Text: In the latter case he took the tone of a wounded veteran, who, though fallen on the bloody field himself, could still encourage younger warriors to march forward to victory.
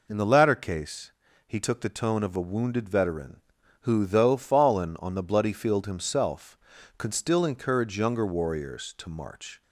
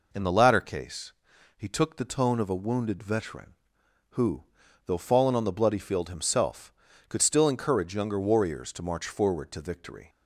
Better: second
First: pauses between "case" and "he"; slight; at 1.1 s; 0.36 s long // stops before "forward to victory"; at 9.6 s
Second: pauses between "case" and "he"; at 1.1 s; 0.44 s long

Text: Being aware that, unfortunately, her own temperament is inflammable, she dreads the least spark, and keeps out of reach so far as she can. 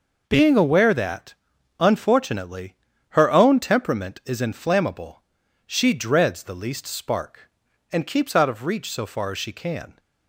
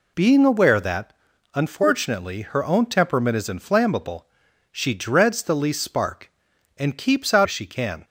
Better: first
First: none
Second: skips "of reach so far"; at 7.4 s

